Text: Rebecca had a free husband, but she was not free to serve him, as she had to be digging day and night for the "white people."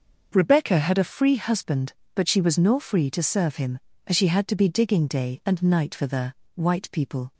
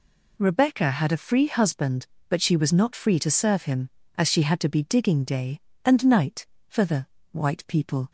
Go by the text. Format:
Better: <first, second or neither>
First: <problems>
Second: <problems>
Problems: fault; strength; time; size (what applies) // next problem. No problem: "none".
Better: second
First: starts louder than the rest; until 1.3 s; 6 dB // says "nor" for "not"; at 2.5 s // pauses between "the" and "white"; slight; at 6.3 s; 0.22 s long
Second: pauses between "the" and "white"; slight; at 7.0 s; 0.24 s long